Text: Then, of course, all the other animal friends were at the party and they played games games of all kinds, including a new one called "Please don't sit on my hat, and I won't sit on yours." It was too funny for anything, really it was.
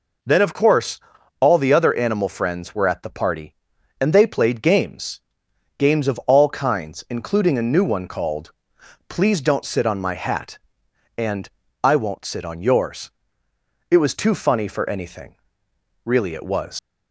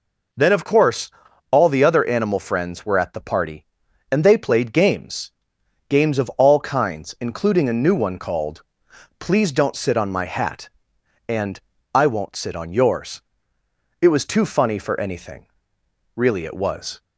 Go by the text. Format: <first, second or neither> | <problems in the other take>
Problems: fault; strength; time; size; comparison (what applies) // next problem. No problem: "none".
second | pauses between "games" and "games"; noticeable; at 5.1 s; 0.60 s long; noticeable in the second // pauses between "called" and "Please"; noticeable; at 8.5 s; 0.58 s long; noticeable in the second // pauses between "and" and "I"; slight; at 11.4 s; 0.34 s long; slight in the second // leaves "was" unfinished; at 16.7 s; 120 ms